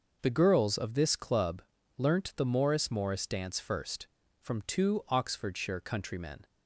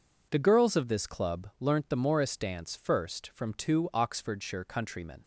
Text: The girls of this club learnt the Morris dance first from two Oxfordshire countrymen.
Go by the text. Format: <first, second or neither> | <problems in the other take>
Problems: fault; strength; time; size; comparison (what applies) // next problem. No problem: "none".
second | pauses between "club" and "learnt"; slight; at 1.6 s; 0.36 s long // says "Morris" twice; at 2.9 s